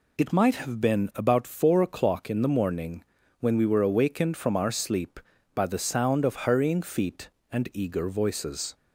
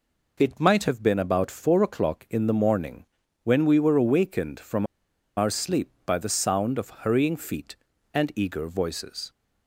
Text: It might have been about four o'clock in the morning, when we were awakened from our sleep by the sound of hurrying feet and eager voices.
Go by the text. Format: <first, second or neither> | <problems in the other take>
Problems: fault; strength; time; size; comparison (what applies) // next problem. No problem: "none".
first | pauses between "from" and "our"; noticeable; at 4.8 s; 0.51 s long